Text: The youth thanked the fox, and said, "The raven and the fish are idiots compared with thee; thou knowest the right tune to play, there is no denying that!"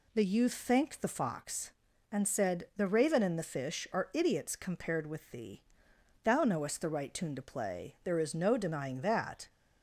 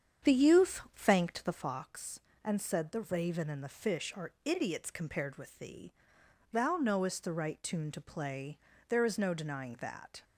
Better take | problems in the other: first | starts louder than the rest; strong; until 1.7 s; 8 dB // pauses between "youth" and "thanked"; slight; at 0.8 s; 0.16 s long

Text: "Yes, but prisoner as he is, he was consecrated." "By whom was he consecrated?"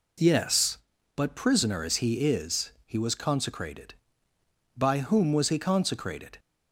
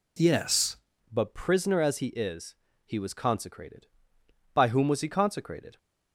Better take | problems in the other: first | changes voice at "but"; from 1.0 s on; 4.7 s long

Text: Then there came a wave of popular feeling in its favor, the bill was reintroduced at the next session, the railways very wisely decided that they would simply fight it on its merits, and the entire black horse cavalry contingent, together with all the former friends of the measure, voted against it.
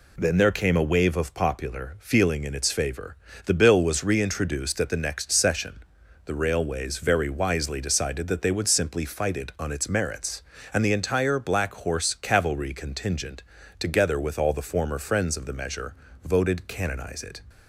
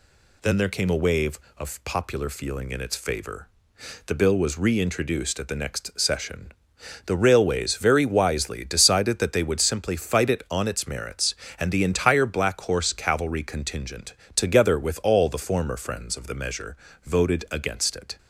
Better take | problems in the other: second | says "canonize" for "against"; at 16.6 s

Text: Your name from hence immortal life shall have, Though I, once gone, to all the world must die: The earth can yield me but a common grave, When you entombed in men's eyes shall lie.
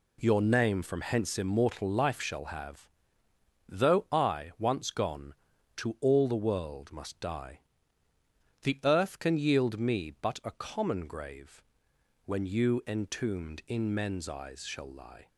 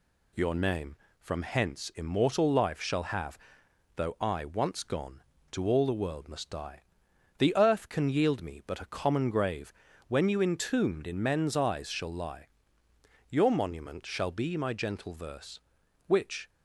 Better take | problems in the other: first | goes on to say "Your monument shall be my gentle verse Which"; strong; from 13.2 s on; 3.2 s long

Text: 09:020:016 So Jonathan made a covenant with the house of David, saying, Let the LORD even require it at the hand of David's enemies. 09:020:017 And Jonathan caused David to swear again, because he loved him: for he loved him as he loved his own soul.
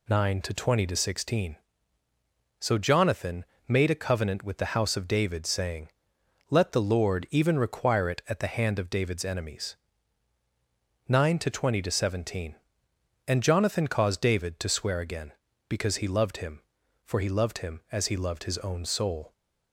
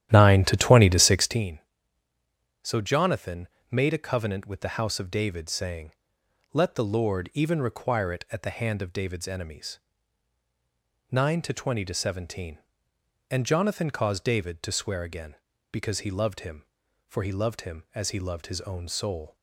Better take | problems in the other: first | starts louder than the rest; strong; until 1.5 s; 11.5 dB // pauses between "Jonathan" and "made"; slight; at 3.4 s; 0.24 s long; slight in the first

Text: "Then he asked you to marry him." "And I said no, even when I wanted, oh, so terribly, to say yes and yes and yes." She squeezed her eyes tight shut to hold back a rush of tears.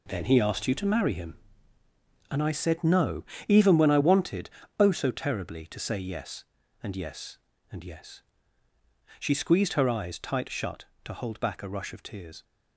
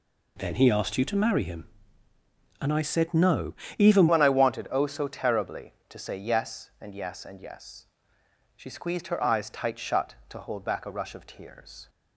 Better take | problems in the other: first | changes voice at "when"; from 4.0 s on; 7.8 s long

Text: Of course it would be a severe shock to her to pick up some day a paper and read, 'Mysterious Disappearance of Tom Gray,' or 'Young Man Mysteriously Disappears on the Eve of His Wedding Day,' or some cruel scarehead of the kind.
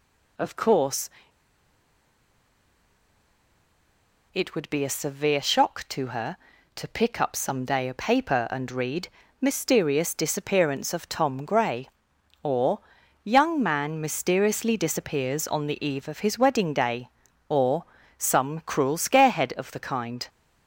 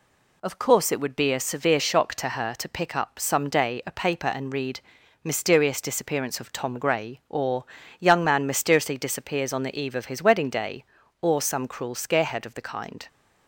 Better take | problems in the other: second | pauses between "course" and "it"; strong; at 1.0 s; 3.2 s long // pauses between "or" and "Young"; at 12.7 s; 0.44 s long; slight in the second // pauses between "or" and "some"; slight; at 17.8 s; 0.32 s long

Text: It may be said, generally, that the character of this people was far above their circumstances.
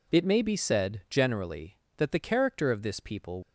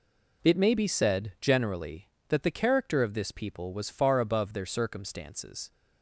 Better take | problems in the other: second | stops before "was far above their circumstances"; at 3.4 s

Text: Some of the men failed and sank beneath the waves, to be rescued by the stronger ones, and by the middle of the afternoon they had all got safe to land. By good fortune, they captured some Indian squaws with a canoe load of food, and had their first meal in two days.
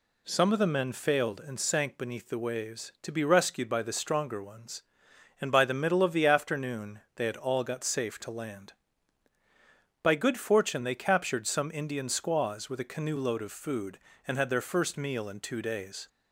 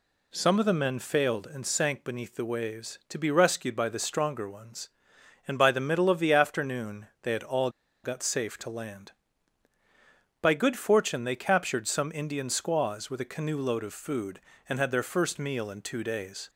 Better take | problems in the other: first | pauses between "afternoon" and "they"; slight; at 7.0 s; 0.16 s long; slight in the first // pauses between "all" and "got"; slight; at 7.6 s; 0.34 s long

